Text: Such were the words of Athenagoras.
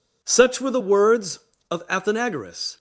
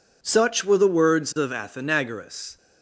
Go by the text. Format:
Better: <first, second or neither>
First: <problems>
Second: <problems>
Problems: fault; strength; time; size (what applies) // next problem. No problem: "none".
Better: neither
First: none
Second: none